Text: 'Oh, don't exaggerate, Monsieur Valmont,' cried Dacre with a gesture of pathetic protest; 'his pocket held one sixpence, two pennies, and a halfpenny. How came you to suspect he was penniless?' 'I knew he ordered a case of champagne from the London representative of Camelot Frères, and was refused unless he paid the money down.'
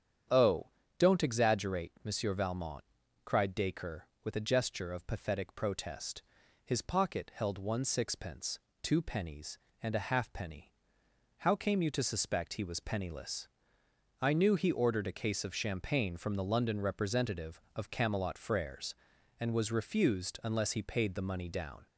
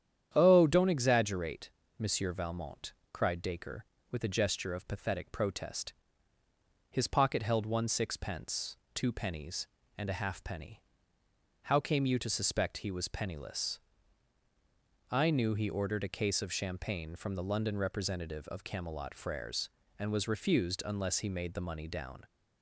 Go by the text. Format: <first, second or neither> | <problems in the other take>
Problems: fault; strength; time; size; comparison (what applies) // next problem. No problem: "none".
first | starts louder than the rest; strong; until 1.3 s; 9.5 dB; strong in the first // says "made" for "paid"; at 21.2 s